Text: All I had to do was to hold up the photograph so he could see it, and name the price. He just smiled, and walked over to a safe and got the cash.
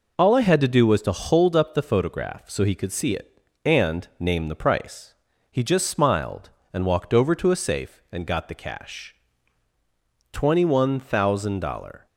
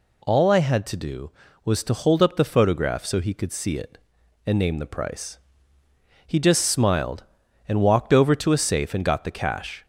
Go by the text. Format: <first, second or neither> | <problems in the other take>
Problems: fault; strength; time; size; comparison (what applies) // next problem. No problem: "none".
second | goes on to say "Twenty one thousand dollar"; strong; from 10.3 s on; 1.7 s long